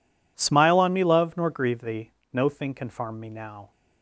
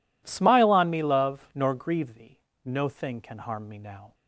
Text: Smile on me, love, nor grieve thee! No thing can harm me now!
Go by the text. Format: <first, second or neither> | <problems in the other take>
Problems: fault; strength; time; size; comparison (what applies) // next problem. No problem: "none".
second | says "farm" for "harm"; at 2.8 s